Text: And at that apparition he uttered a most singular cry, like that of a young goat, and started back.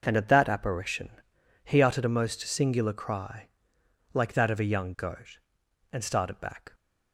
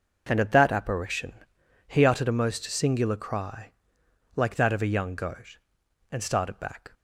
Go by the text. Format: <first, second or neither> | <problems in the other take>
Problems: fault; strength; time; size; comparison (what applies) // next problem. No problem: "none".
neither | pauses between "apparition" and "he"; noticeable; the same in both